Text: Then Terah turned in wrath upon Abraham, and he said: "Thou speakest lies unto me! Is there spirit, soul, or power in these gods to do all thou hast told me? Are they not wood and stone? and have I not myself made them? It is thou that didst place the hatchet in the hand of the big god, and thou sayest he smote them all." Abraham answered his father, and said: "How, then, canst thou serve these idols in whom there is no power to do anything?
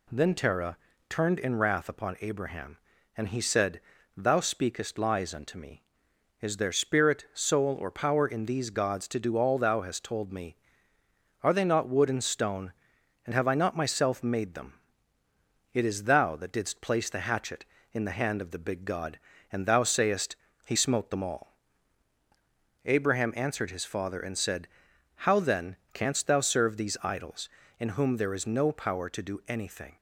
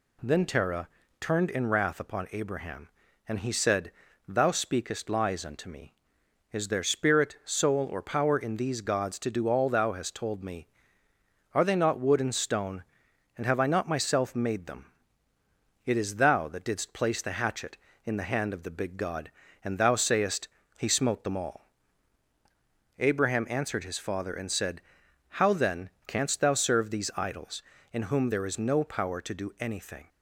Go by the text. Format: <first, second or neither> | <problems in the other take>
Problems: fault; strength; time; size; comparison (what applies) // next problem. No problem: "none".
neither | pauses between "Terah" and "turned"; slight; the same in both // pauses between "sayest" and "he"; slight; the same in both